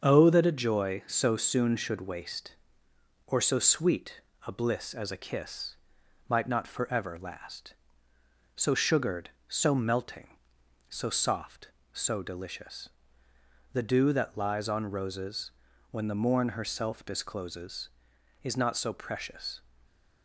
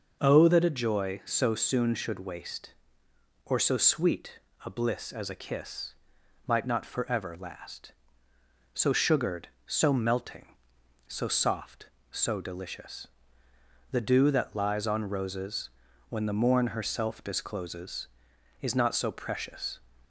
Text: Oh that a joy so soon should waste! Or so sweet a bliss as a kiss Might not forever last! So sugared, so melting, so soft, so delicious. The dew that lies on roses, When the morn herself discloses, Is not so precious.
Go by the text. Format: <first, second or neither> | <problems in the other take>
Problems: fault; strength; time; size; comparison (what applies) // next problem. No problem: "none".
second | gets quieter; noticeable; throughout; 4.5 dB // pauses between "sweet" and "a"; slight; at 4.2 s; 0.26 s long; slight in the second // pauses between "kiss" and "Might"; noticeable; at 5.7 s; 0.54 s long; noticeable in the second // stays silent after the last word; slight; from 19.5 s on; 0.7 s long